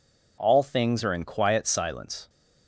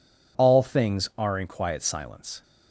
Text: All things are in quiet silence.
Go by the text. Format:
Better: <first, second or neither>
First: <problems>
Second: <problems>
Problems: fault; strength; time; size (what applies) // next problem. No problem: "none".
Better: neither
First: none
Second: none